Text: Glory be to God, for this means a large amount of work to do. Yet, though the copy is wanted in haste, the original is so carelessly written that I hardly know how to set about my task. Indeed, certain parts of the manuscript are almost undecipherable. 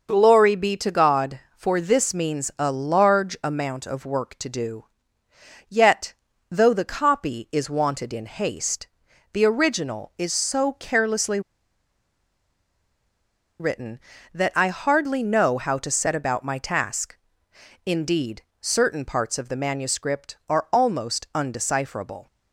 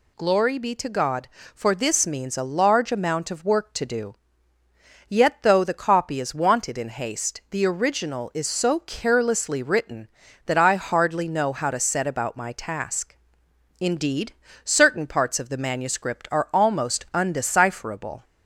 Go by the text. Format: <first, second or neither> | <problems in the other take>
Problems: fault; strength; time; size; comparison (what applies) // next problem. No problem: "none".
second | pauses between "carelessly" and "written"; strong; at 11.3 s; 2.1 s long